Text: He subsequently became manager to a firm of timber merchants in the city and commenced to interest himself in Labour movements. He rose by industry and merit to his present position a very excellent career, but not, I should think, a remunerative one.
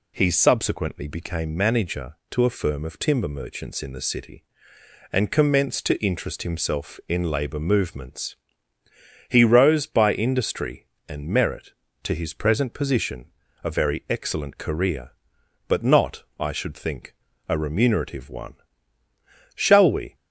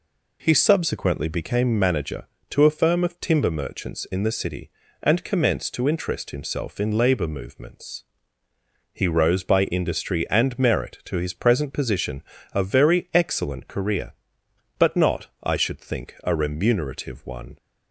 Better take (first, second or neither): second